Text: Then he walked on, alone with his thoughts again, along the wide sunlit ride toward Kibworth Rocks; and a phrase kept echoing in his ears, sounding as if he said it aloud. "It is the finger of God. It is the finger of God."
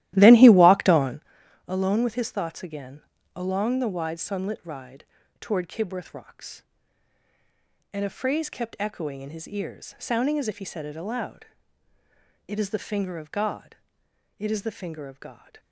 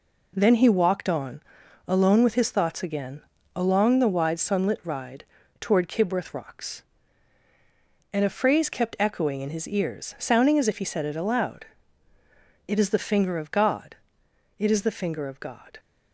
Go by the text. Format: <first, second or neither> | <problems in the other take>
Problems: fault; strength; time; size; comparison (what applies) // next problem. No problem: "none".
second | starts louder than the rest; strong; until 1.3 s; 14.5 dB // pauses between "ride" and "toward"; slight; at 5.0 s; 0.36 s long; slight in the second